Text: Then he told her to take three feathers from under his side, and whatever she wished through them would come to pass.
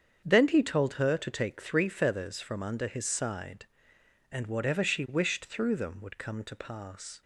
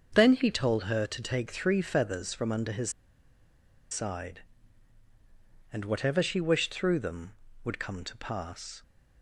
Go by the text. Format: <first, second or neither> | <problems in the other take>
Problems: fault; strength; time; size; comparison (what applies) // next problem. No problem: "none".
first | starts louder than the rest; until 1.1 s; 6.5 dB; strong in the first // pauses between "his" and "side"; at 2.9 s; 0.99 s long